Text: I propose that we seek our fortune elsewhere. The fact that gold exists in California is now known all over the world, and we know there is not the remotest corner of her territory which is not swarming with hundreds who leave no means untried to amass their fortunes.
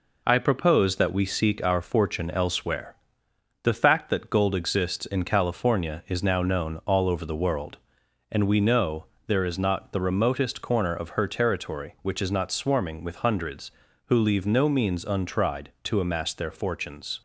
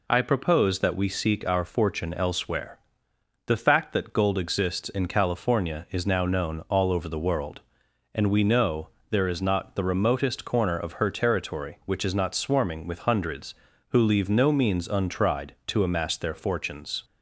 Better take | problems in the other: second | gets quieter; throughout; 3.5 dB // pauses between "know" and "there"; slight; at 9.0 s; 0.20 s long; slight in the second

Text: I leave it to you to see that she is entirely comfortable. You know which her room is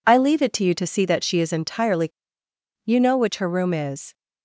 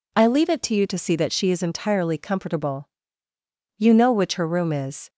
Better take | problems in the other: second | skips "comfortable"; at 2.4 s

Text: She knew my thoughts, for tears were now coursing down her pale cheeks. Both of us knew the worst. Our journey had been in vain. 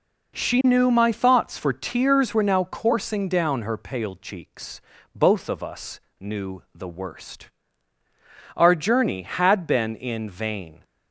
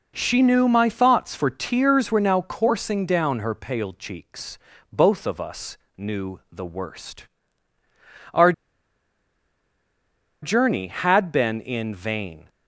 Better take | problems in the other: first | pauses between "us" and "knew"; slight; at 5.7 s; 0.20 s long; slight in the first // pauses between "Our" and "journey"; strong; at 8.5 s; 1.8 s long

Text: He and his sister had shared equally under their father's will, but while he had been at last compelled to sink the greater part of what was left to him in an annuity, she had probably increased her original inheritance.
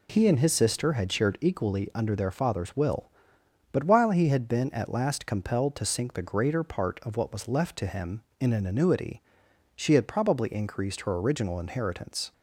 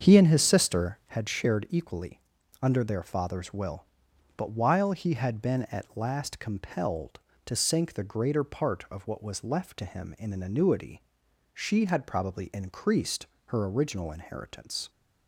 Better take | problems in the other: first | starts louder than the rest; strong; until 1.1 s; 7 dB // pauses between "equally" and "under"; at 2.2 s; 0.38 s long // pauses between "increased" and "her"; slight; at 13.2 s; 0.22 s long

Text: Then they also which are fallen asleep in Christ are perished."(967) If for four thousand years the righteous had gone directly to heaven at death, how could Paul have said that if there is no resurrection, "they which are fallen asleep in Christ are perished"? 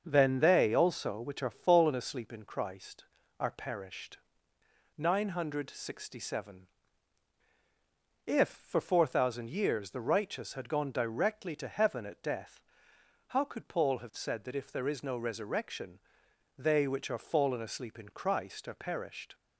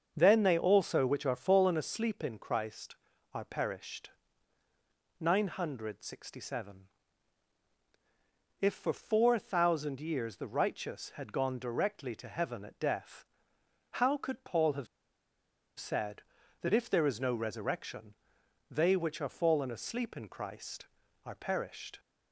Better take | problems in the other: first | starts louder than the rest; strong; until 1.1 s; 7 dB; strong in the first // pauses between "have" and "said"; noticeable; at 14.8 s; 0.92 s long

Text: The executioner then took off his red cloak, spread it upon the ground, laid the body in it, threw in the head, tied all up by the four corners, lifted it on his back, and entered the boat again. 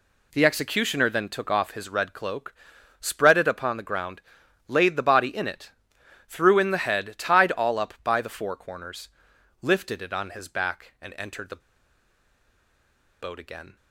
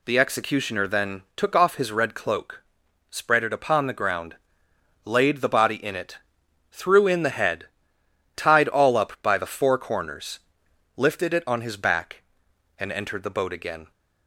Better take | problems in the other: second | pauses between "the" and "boat"; strong; at 11.6 s; 1.6 s long

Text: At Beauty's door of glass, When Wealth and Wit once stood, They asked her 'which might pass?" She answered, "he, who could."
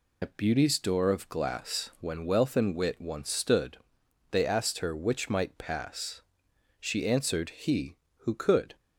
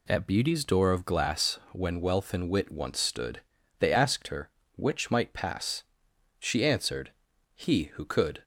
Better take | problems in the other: second | loses the start of "At"; at 0.2 s; 95 ms

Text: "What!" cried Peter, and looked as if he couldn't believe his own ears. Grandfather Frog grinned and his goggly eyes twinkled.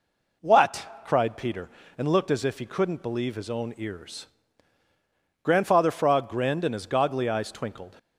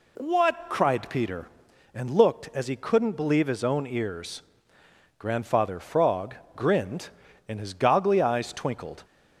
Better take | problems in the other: first | skips "if"; at 2.6 s // pauses between "Frog" and "grinned"; slight; at 6.3 s; 0.20 s long

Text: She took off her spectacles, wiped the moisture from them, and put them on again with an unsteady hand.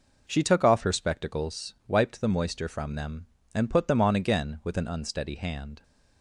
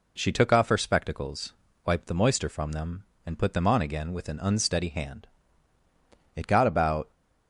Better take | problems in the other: first | goes on to say "It got about"; noticeable; from 6.3 s on; 0.76 s long

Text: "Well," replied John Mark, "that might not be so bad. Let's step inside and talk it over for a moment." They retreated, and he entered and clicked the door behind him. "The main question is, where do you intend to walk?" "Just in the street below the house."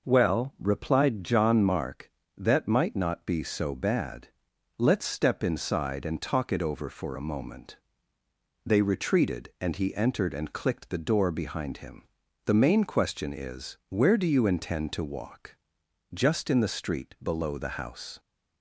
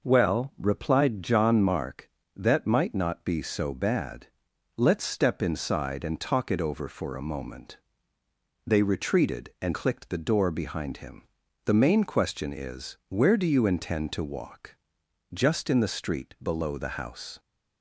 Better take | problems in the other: first | skips "he entered and"; at 9.7 s

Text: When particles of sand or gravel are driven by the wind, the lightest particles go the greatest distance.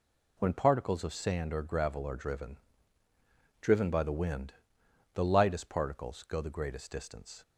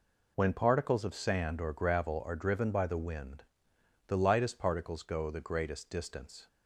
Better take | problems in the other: second | says "driven" twice; at 3.6 s

